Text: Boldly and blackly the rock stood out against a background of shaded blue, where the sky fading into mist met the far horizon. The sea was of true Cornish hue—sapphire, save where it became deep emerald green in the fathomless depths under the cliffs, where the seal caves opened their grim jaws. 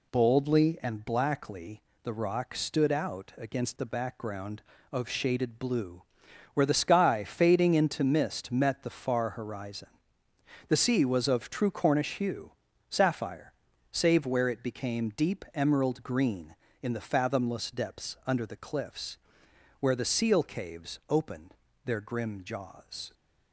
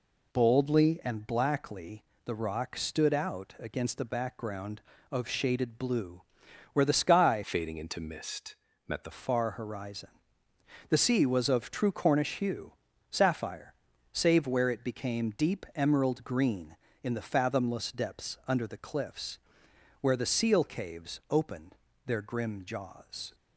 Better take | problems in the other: first | pauses between "blackly" and "the"; slight; at 2.0 s; 0.22 s long; slight in the first // changes voice from "fading" to "the"; from 7.4 to 9.1 s; 1.7 s long // pauses between "mist" and "met"; slight; at 8.5 s; 0.32 s long // pauses between "opened" and "their"; slight; at 21.7 s; 0.32 s long; slight in the first

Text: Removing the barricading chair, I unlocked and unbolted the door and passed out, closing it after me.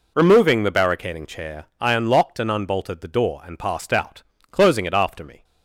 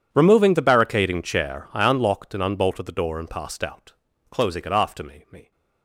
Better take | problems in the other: first | says "me" twice; at 5.3 s

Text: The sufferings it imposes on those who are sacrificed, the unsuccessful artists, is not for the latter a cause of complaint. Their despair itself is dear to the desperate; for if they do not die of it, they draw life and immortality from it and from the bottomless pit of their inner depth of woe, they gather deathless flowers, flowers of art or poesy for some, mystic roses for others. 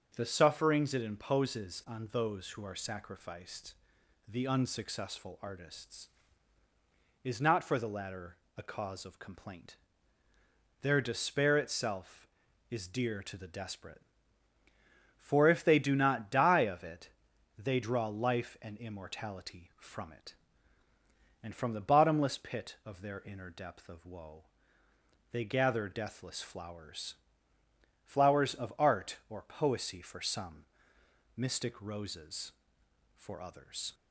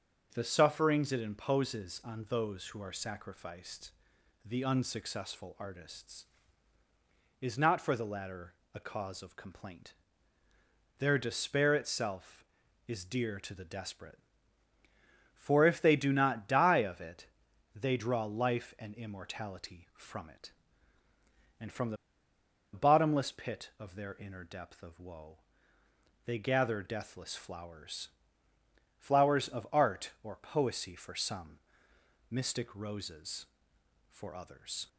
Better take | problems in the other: first | starts louder than the rest; until 1.3 s; 6.5 dB; also in the first // pauses between "latter" and "a"; slight; at 8.5 s; 0.20 s long; slight in the first // pauses between "the" and "bottomless"; noticeable; at 21.9 s; 0.77 s long

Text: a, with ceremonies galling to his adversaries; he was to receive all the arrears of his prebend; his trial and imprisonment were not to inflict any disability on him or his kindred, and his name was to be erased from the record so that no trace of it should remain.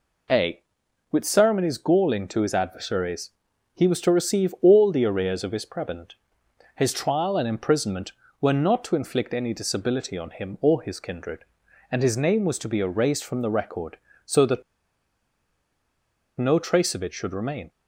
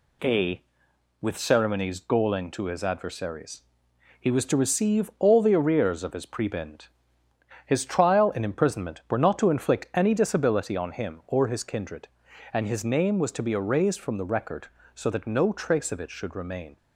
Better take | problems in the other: second | pauses between "that" and "no"; strong; at 14.6 s; 1.7 s long

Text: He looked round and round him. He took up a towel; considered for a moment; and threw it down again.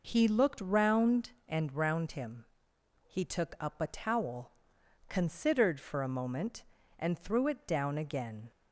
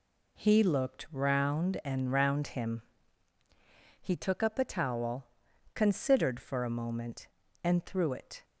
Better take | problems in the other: first | stops before "down again"; at 8.4 s

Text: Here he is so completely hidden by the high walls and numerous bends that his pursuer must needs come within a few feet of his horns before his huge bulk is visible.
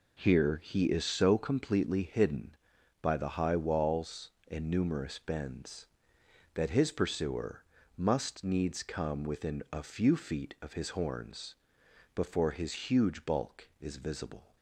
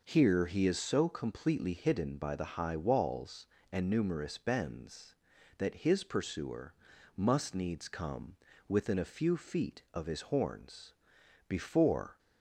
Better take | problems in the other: first | pauses between "pursuer" and "must"; at 6.7 s; 0.42 s long; slight in the first // pauses between "come" and "within"; slight; at 8.3 s; 0.32 s long // pauses between "horns" and "before"; noticeable; at 10.9 s; 0.56 s long; noticeable in the first // stops before "his huge bulk is visible"; at 12.1 s

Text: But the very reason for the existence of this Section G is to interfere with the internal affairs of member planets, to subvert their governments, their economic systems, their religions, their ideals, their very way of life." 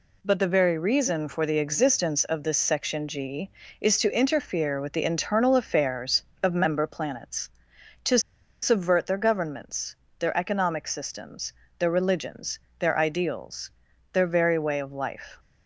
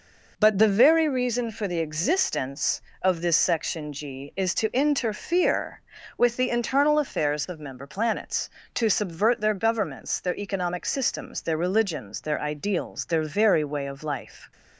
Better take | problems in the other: second | pauses between "to" and "subvert"; at 8.1 s; 0.43 s long

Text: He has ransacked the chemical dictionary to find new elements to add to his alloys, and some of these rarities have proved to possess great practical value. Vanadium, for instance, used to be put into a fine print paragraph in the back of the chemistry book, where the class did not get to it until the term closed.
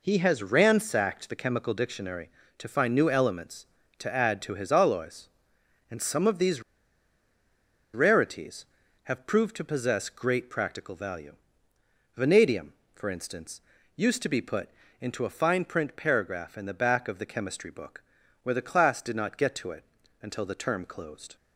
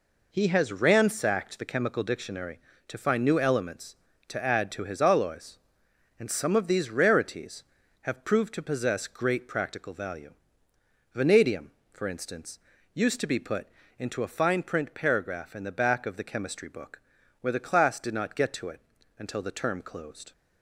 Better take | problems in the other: second | pauses between "these" and "rarities"; strong; at 6.6 s; 1.3 s long // pauses between "put" and "into"; slight; at 14.6 s; 0.32 s long; slight in the second // pauses between "it" and "until"; at 19.8 s; 0.38 s long; also in the second

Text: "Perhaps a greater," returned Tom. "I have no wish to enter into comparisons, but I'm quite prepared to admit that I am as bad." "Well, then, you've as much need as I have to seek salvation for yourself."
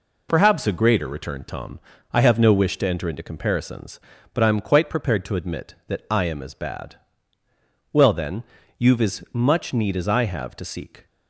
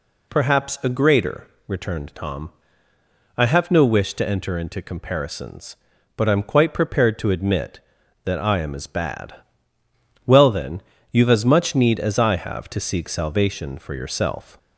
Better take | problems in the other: second | stops before "salvation for yourself"; at 11.0 s

